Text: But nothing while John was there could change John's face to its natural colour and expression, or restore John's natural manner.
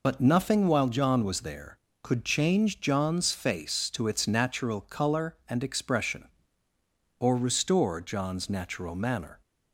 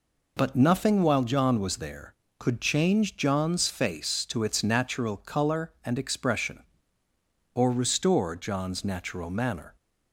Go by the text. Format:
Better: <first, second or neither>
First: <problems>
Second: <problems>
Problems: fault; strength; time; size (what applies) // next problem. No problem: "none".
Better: second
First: loses the start of "But"; at 0.0 s; 35 ms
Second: none